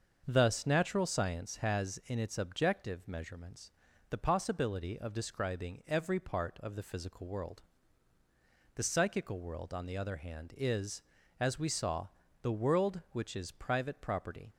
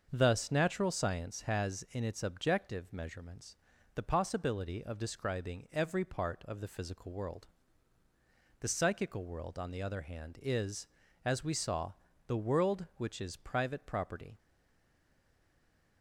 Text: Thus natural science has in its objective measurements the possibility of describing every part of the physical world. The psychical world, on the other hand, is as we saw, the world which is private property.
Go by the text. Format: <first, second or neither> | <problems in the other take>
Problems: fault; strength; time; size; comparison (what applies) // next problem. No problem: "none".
first | starts louder than the rest; until 1.1 s; 6.5 dB; also in the first // pauses between "measurements" and "the"; at 3.5 s; 0.38 s long; also in the first // stays silent after the last word; noticeable; from 14.3 s on; 1.7 s long